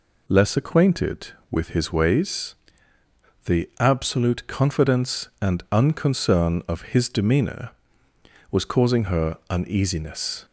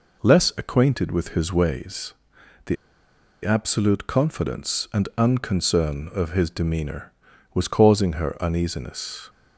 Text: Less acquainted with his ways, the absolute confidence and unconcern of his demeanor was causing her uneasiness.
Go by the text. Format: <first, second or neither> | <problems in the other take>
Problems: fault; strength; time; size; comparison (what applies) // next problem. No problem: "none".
first | pauses between "the" and "absolute"; noticeable; at 2.7 s; 0.67 s long